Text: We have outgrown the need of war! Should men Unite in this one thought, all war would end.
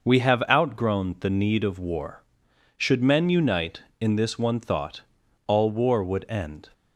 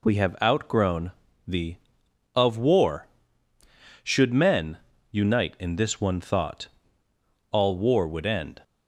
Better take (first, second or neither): first